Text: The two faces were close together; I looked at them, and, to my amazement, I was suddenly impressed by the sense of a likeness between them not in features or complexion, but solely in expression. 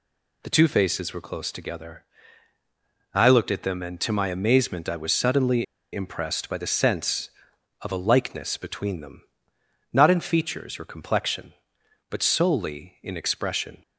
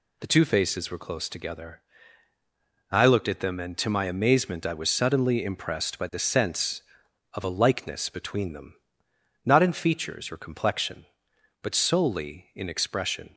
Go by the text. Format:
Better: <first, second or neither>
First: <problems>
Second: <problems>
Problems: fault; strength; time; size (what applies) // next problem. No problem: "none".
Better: second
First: pauses between "suddenly" and "impressed"; slight; at 5.6 s; 0.28 s long // pauses between "them" and "not"; noticeable; at 9.2 s; 0.72 s long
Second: pauses between "them" and "not"; noticeable; at 8.7 s; 0.72 s long